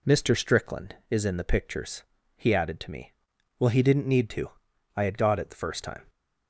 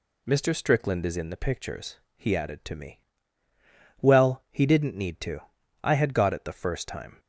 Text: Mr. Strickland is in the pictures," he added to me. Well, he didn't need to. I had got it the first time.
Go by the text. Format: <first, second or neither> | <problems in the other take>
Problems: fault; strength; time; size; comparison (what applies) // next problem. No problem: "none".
neither | none